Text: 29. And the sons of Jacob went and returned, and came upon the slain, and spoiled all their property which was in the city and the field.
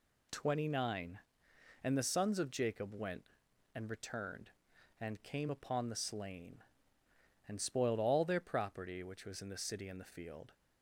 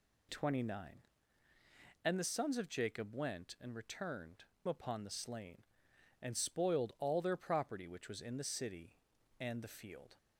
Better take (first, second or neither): first